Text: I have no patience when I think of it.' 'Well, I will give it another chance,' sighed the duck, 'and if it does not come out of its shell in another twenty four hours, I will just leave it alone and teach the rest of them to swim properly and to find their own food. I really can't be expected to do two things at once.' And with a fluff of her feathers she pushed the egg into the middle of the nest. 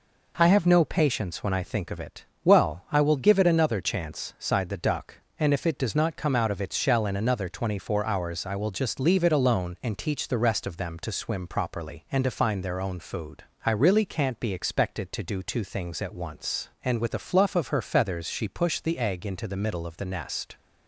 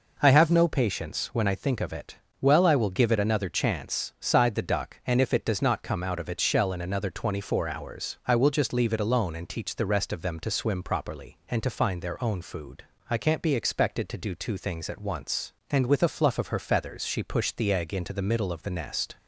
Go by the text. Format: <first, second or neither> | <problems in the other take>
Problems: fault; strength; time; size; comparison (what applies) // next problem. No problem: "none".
first | skips "really"; at 13.1 s